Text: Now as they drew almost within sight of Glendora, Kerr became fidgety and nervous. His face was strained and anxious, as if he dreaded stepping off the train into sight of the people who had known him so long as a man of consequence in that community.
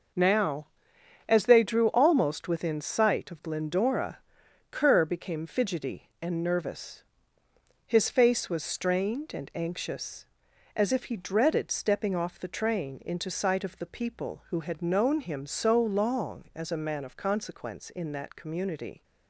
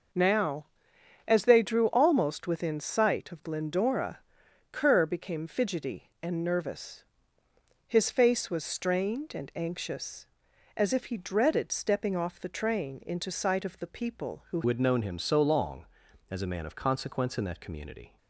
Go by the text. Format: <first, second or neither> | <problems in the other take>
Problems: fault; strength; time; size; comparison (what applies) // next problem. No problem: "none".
first | changes voice at "had"; from 14.6 s on; 3.5 s long